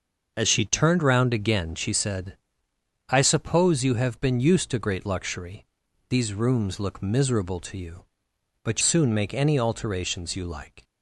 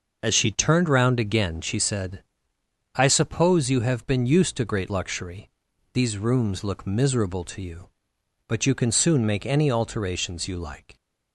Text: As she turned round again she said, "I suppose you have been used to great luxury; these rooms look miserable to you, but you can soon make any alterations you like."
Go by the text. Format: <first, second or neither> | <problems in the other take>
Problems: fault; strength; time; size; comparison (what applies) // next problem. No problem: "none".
second | starts louder than the rest; noticeable; until 1.3 s; 6 dB; noticeable in the second // skips "you can"; at 8.8 s